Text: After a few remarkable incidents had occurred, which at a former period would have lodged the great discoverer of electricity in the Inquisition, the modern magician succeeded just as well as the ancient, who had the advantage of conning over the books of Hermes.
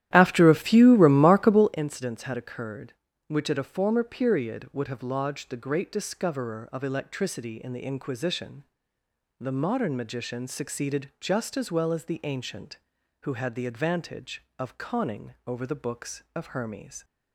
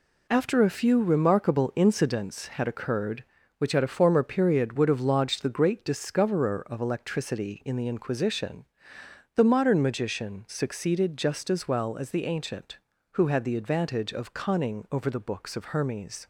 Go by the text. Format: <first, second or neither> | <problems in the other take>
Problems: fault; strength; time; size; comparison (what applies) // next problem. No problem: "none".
second | starts louder than the rest; strong; until 1.8 s; 12.5 dB